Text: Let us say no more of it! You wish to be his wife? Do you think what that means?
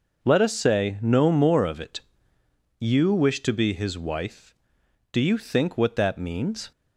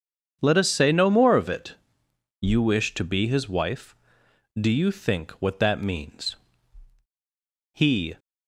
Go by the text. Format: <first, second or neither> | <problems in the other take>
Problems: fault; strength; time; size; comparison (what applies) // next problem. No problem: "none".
first | starts louder than the rest; strong; until 1.4 s; 7.5 dB // goes on to say "He"; slight; from 7.7 s on; 0.44 s long